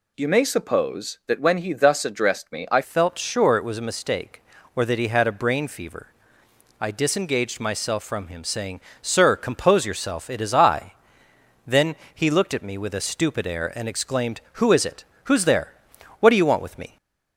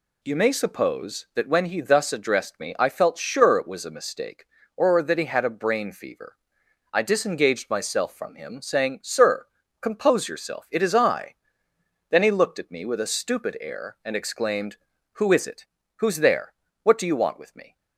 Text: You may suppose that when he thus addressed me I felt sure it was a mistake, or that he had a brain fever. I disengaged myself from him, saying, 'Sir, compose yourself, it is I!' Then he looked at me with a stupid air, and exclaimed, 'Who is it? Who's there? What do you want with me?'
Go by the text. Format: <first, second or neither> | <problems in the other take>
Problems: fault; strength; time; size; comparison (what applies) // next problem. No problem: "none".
second | changes voice at "felt"; from 2.8 s on; 14.1 s long // pauses between "Then" and "he"; slight; at 11.9 s; 0.18 s long // stays silent after the last word; slight; from 16.8 s on; 0.5 s long